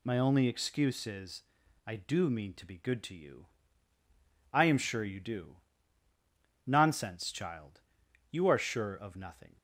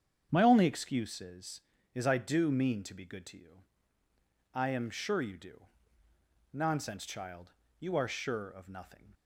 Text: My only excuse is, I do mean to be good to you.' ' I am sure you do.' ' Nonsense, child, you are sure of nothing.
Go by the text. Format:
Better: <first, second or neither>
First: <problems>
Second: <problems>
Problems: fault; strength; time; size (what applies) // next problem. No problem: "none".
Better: first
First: none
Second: starts louder than the rest; strong; until 1.3 s; 8.5 dB // says "is" twice; at 1.9 s